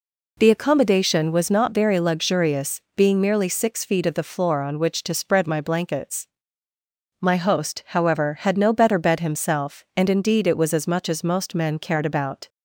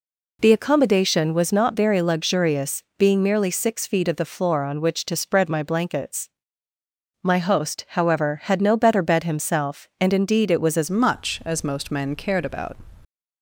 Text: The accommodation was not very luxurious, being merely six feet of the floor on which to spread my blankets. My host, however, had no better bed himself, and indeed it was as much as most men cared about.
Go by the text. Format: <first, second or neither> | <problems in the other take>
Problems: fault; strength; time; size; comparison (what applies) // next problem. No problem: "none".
first | changes voice at "much"; from 10.8 s on; 1.9 s long